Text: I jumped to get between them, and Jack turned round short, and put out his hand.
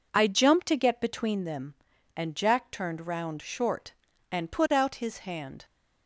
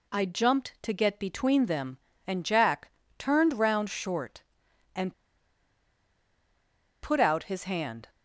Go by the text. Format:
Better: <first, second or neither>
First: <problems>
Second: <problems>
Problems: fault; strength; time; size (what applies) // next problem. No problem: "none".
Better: first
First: none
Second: pauses between "Jack" and "turned"; slight; at 2.8 s; 0.28 s long // pauses between "and" and "put"; strong; at 5.1 s; 1.8 s long